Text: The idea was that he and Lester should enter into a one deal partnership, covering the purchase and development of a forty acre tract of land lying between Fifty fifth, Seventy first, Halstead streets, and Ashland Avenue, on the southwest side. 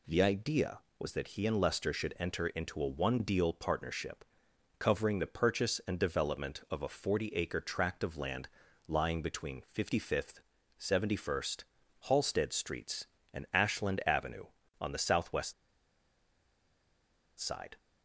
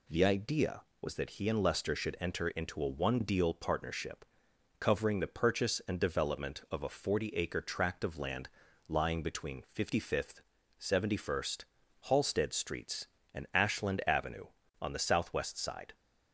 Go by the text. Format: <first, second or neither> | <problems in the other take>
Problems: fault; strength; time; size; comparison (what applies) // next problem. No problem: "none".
second | pauses between "land" and "lying"; at 8.4 s; 0.38 s long; also in the second // pauses between "southwest" and "side"; strong; at 15.5 s; 1.8 s long